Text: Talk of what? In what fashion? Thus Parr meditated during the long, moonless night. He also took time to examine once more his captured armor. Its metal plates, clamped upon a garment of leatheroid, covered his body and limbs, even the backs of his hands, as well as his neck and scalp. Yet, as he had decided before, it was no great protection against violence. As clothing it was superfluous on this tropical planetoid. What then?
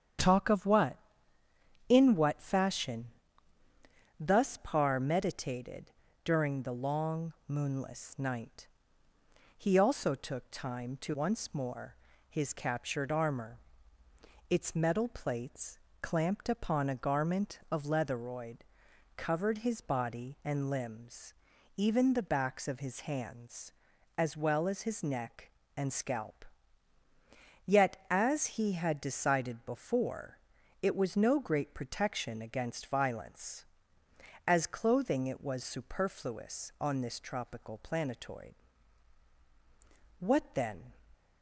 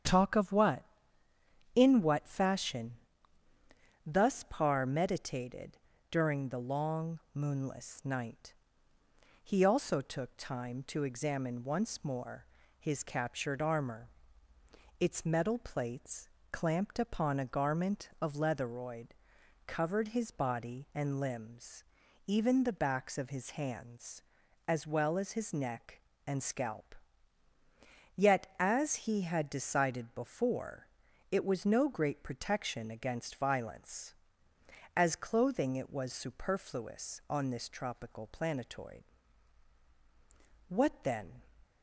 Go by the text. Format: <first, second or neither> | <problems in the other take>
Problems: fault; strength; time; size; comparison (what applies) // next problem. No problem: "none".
second | starts louder than the rest; strong; until 2.1 s; 9 dB; strong in the second // pauses between "meditated" and "during"; slight; at 5.9 s; 0.34 s long; slight in the second // skips "examine"; at 11.1 s // pauses between "more" and "his"; slight; at 11.9 s; 0.32 s long; slight in the second